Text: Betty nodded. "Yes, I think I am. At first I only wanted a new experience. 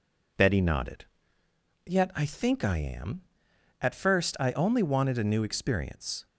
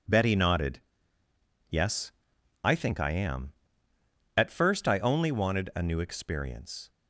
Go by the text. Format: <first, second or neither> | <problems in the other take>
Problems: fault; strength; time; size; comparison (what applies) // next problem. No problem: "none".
second | says "Yet" for "Yes"; at 1.8 s